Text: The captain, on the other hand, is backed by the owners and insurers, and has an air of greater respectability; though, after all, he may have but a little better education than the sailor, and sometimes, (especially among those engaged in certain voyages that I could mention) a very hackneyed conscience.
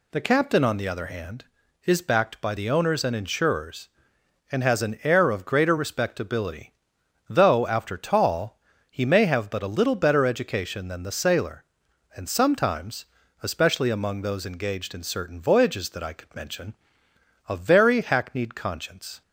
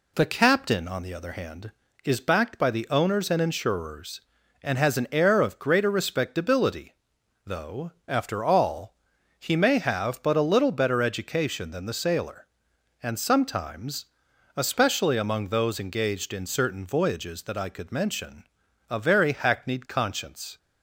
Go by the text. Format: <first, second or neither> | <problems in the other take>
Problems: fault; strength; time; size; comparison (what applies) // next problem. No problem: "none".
second | says "tall" for "all"; at 7.9 s